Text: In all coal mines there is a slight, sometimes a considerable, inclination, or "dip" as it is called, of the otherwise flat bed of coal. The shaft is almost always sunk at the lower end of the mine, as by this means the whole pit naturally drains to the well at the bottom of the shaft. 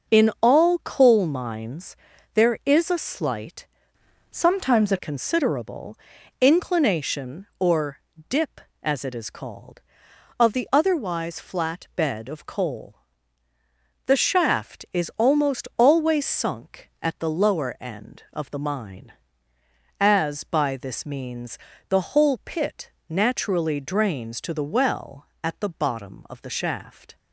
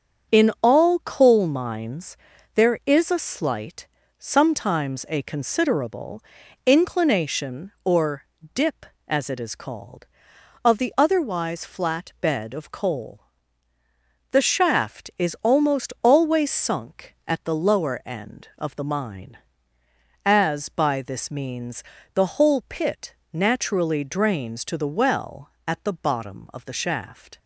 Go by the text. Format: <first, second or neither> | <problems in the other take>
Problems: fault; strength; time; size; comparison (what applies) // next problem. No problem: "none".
second | starts louder than the rest; noticeable; until 1.2 s; 6 dB; also in the second // pauses between "mines" and "there"; slight; at 1.9 s; 0.36 s long; slight in the second // changes voice from "sometimes" to "a"; from 4.3 to 4.9 s; 0.6 s long // pauses between "or" and "dip"; slight; at 7.9 s; 0.30 s long; slight in the second // pauses between "means" and "the"; slight; at 21.5 s; 0.32 s long; slight in the second // pauses between "pit" and "naturally"; slight; at 22.9 s; 0.18 s long; slight in the second